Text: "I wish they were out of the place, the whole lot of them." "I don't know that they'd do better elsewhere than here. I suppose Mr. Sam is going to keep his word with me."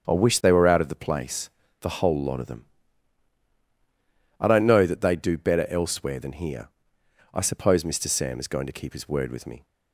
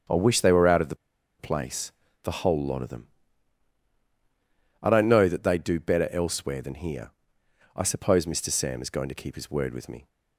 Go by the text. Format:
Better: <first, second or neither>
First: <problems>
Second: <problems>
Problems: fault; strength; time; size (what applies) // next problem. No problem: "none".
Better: first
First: starts louder than the rest; strong; until 1.1 s; 7.5 dB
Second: starts louder than the rest; strong; until 1.5 s; 7.5 dB // pauses between "the" and "place"; at 0.9 s; 0.43 s long